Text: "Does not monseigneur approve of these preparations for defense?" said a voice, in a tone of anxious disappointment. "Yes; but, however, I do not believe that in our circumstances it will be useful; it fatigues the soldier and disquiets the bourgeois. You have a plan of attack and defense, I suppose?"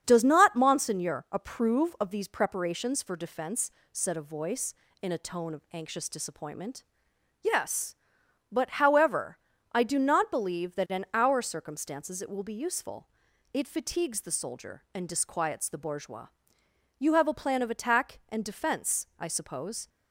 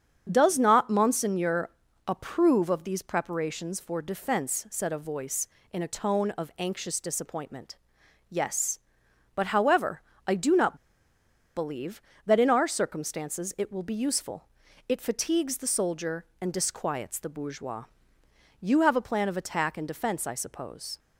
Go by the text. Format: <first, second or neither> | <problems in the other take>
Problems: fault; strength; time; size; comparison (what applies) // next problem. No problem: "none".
first | starts louder than the rest; strong; until 1.3 s; 7.5 dB; strong in the first // pauses between "monseigneur" and "approve"; slight; at 1.6 s; 0.36 s long // pauses between "not" and "believe"; noticeable; at 10.7 s; 0.80 s long